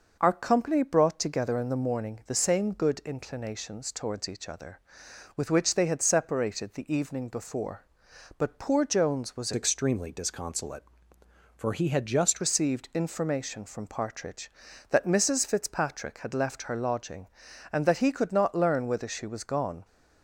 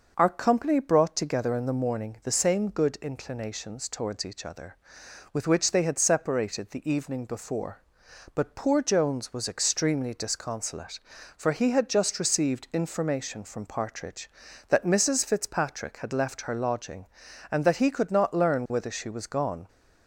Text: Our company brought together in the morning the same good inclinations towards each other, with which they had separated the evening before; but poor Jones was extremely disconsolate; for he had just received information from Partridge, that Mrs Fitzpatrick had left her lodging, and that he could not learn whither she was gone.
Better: second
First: changes voice from "extremely" to "just"; from 9.5 to 12.4 s; 2.9 s long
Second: none

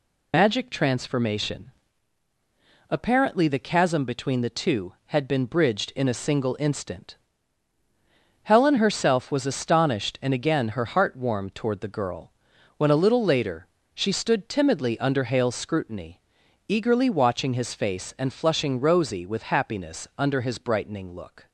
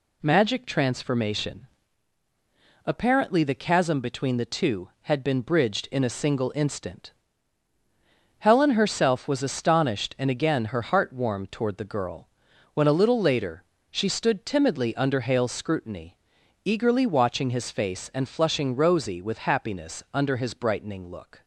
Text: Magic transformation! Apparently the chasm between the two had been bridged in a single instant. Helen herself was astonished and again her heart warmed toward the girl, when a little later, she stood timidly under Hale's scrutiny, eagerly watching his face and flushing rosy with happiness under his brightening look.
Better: second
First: loses the start of "Magic"; at 0.3 s; 75 ms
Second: none

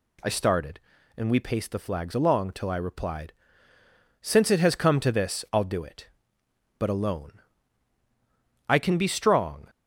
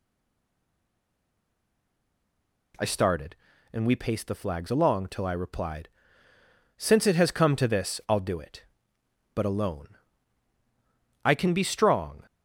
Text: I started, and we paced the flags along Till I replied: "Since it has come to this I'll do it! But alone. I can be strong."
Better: first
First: none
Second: stays silent before the first word; strong; until 2.7 s; 2.7 s long

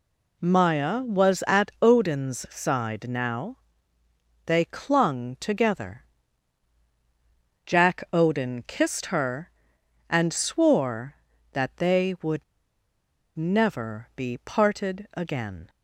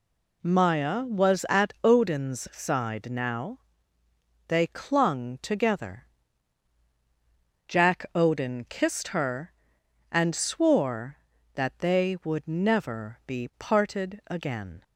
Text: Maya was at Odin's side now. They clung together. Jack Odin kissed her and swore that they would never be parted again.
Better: second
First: pauses between "would" and "never"; noticeable; at 12.4 s; 0.93 s long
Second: none

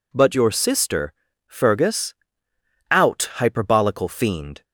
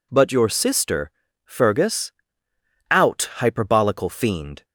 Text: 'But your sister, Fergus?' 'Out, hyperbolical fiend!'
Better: neither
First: none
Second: none

